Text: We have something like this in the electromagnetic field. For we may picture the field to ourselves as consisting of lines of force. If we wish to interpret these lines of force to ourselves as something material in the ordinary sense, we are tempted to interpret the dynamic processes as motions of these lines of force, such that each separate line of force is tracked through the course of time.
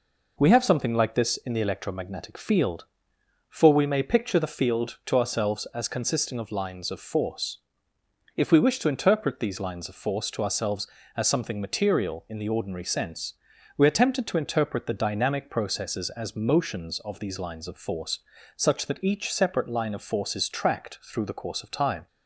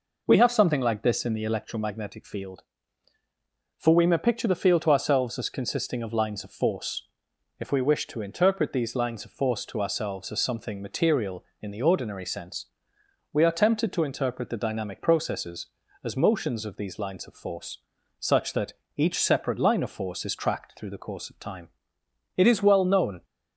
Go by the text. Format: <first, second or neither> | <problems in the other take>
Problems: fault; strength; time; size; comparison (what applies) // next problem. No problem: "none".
first | pauses between "that" and "each"; slight; at 18.7 s; 0.24 s long // goes on to say "It is well known"; noticeable; from 22.3 s on; 0.88 s long